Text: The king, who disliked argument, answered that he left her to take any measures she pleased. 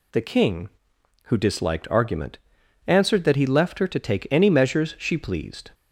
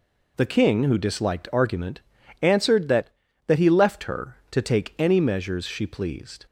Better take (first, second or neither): first